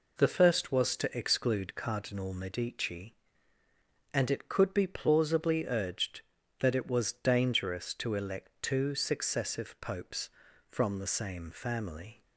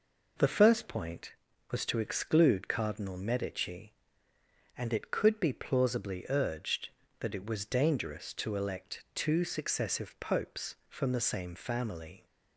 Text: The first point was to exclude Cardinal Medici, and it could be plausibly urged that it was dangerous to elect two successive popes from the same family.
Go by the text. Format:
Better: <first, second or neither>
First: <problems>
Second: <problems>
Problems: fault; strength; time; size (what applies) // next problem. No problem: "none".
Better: second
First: skips "point"; at 0.7 s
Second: none